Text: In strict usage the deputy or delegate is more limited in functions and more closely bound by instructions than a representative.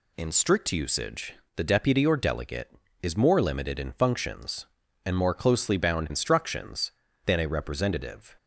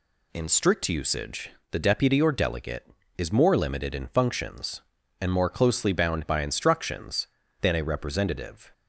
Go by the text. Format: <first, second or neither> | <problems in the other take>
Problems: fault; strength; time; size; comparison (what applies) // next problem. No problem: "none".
second | pauses between "usage" and "the"; slight; at 1.3 s; 0.22 s long; slight in the second // skips "by"; at 6.1 s